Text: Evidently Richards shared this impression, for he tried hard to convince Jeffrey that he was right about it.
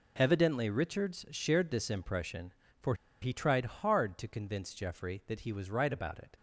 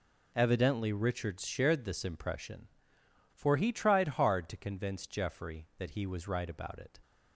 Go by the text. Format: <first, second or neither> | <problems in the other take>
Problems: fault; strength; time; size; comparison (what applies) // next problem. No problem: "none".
second | pauses between "for" and "he"; slight; at 2.9 s; 0.27 s long